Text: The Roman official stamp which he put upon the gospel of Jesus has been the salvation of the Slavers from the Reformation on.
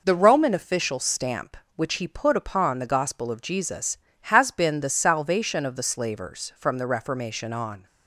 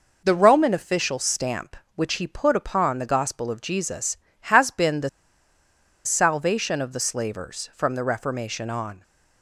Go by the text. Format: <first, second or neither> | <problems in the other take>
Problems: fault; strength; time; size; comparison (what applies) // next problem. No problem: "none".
first | pauses between "the" and "salvation"; noticeable; at 5.0 s; 0.96 s long